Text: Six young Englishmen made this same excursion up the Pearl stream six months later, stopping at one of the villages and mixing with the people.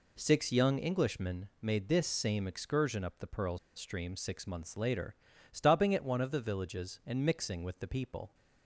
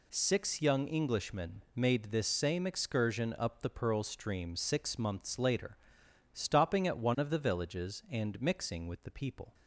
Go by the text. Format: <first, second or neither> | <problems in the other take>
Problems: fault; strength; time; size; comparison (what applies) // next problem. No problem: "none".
second | pauses between "Pearl" and "stream"; slight; at 3.5 s; 0.17 s long